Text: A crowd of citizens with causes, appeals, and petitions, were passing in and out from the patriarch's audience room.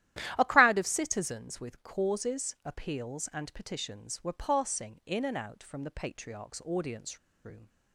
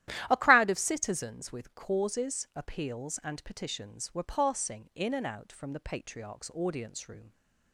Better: second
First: starts louder than the rest; strong; until 1.4 s; 12.5 dB // pauses between "audience" and "room"; slight; at 7.1 s; 0.26 s long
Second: starts louder than the rest; strong; until 1.3 s; 12.5 dB

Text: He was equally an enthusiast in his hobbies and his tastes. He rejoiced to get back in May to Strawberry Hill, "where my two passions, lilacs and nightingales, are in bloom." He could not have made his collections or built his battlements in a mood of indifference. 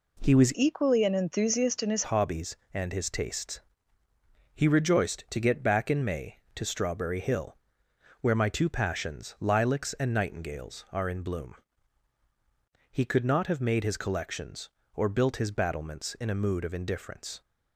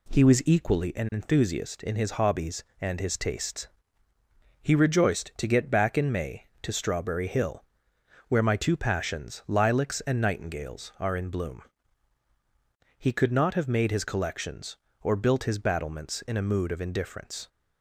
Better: second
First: changes voice from "equally" to "his"; from 0.5 to 2.0 s; 1.5 s long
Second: none

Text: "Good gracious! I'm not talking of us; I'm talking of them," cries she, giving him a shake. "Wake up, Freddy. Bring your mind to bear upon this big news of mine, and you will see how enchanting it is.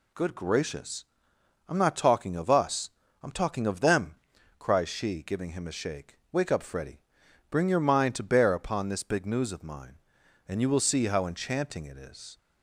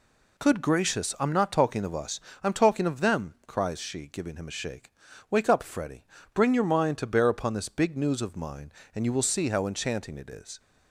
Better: neither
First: none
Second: none

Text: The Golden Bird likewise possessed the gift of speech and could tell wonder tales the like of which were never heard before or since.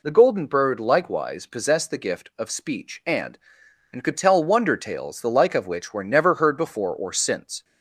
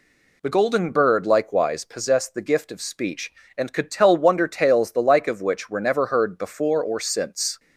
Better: second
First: says "and" twice; at 3.9 s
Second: none

